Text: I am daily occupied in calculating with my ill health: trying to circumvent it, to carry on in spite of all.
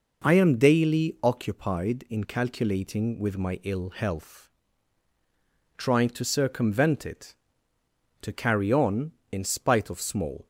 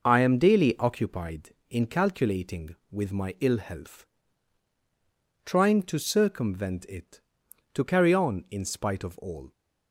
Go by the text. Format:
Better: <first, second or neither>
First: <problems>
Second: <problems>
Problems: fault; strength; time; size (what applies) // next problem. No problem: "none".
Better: second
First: says "small" for "all"; at 9.9 s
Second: none